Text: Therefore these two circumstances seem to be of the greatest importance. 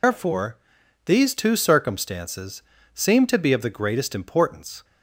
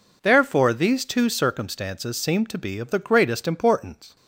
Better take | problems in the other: second | loses the start of "Therefore"; at 0.0 s; 155 ms // pauses between "Therefore" and "these"; noticeable; at 0.5 s; 0.50 s long // pauses between "circumstances" and "seem"; slight; at 2.6 s; 0.32 s long

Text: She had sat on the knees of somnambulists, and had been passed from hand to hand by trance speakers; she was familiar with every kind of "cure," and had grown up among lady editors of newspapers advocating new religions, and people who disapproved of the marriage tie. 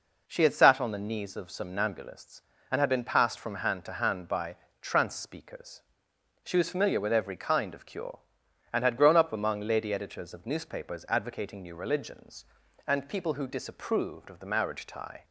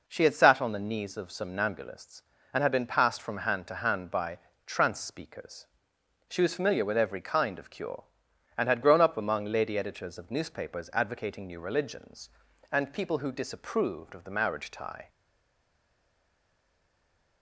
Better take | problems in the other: first | pauses between "by" and "trance"; slight; at 4.3 s; 0.26 s long; slight in the first // stays silent after the last word; from 15.0 s on; 2.4 s long

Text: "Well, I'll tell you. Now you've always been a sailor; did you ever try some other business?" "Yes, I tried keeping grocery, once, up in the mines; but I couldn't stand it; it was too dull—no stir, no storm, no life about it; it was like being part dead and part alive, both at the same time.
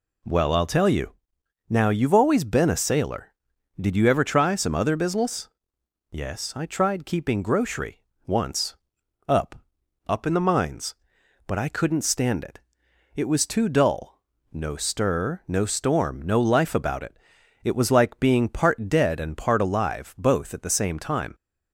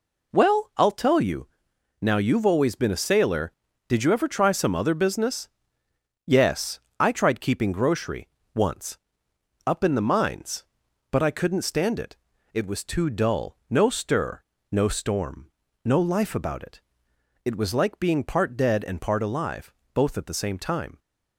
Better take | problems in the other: second | says "up" twice; at 10.0 s

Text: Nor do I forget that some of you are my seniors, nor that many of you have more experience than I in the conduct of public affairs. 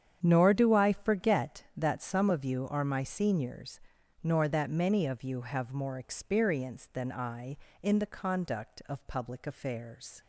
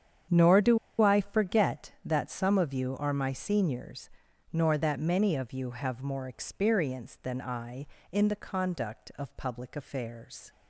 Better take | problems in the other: first | starts louder than the rest; strong; until 1.5 s; 8.5 dB; strong in the first // pauses between "do" and "I"; slight; at 0.7 s; 0.23 s long

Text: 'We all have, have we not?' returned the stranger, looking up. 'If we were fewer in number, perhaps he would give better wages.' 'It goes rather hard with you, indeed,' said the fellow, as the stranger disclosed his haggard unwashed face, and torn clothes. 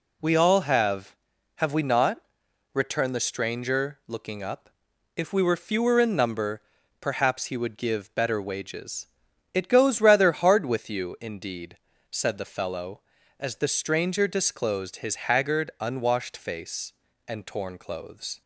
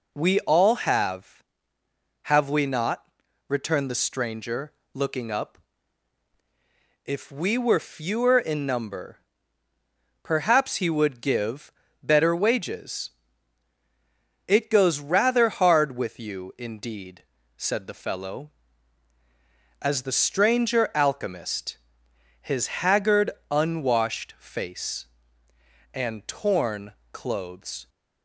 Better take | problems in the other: first | pauses between "give" and "better"; slight; at 11.7 s; 0.32 s long // says "alchemist" for "disclosed"; at 20.9 s // pauses between "haggard" and "unwashed"; slight; at 23.2 s; 0.22 s long // pauses between "torn" and "clothes"; slight; at 26.9 s; 0.18 s long

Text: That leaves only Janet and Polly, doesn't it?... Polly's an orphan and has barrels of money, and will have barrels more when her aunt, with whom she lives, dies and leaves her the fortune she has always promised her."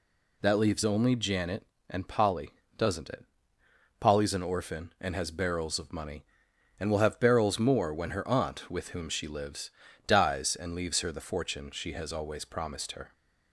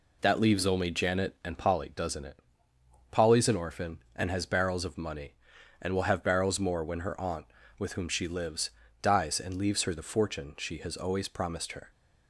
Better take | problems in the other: neither | none

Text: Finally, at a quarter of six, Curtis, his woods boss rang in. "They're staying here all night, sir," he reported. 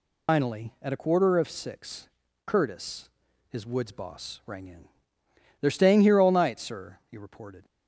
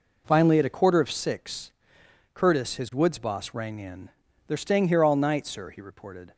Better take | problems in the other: second | loses the start of "Finally"; at 0.2 s; 125 ms

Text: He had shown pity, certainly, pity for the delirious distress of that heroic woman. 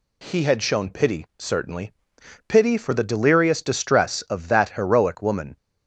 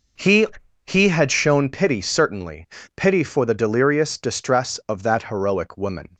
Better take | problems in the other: first | says "He" twice; at 0.8 s

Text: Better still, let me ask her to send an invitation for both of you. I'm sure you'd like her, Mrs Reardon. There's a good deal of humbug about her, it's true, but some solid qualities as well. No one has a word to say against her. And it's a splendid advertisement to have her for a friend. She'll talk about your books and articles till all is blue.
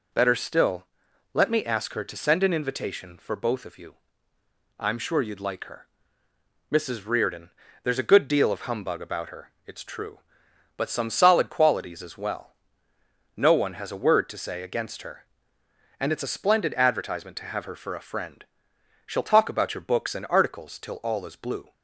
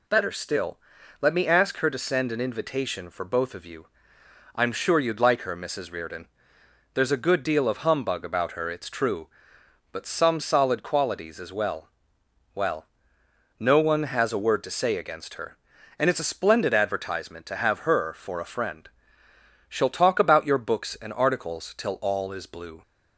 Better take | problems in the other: first | says "well" twice; at 12.5 s

